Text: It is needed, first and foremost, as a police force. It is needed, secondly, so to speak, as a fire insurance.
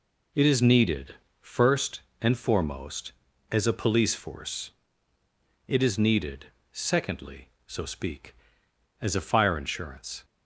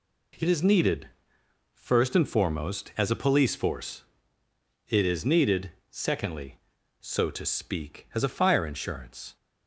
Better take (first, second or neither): second